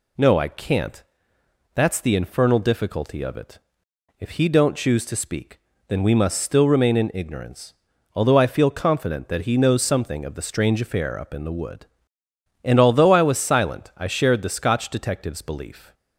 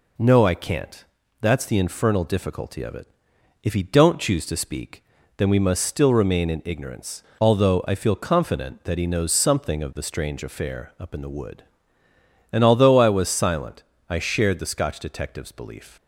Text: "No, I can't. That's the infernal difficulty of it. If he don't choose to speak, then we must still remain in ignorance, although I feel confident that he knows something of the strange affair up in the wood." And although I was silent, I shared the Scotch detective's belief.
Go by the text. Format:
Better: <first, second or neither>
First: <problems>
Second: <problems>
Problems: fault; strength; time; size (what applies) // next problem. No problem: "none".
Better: neither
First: none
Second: none